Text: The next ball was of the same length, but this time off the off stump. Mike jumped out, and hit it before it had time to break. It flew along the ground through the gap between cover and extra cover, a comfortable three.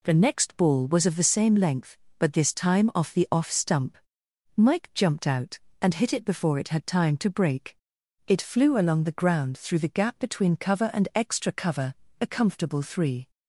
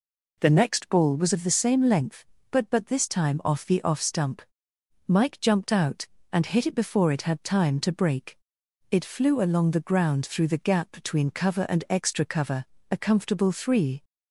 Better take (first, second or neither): first